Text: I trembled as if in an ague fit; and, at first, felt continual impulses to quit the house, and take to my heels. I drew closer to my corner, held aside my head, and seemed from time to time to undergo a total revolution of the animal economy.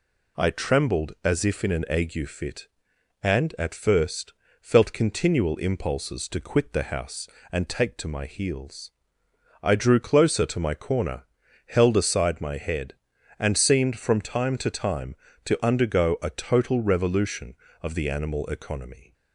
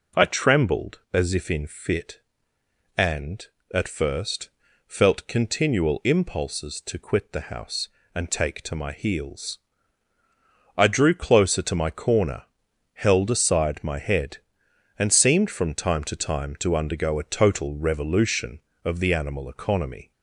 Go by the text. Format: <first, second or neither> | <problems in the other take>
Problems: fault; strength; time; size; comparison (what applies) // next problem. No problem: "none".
first | skips "an ague"; at 1.6 s